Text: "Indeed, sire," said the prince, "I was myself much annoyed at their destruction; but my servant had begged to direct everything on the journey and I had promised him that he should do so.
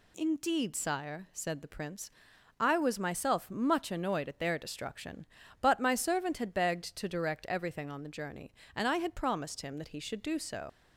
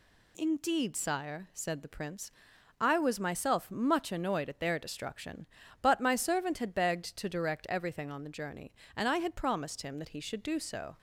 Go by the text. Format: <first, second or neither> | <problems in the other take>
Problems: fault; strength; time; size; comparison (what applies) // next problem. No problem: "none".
second | leaves "so" unfinished; at 10.6 s; 75 ms